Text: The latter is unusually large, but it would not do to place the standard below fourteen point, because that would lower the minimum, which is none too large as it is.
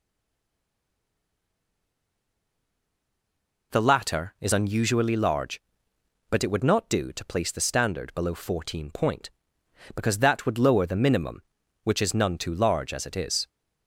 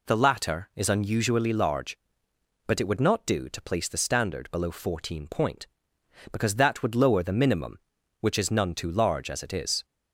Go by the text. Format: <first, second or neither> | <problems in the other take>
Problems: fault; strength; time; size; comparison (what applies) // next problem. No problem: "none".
second | stays silent before the first word; strong; until 3.7 s; 3.7 s long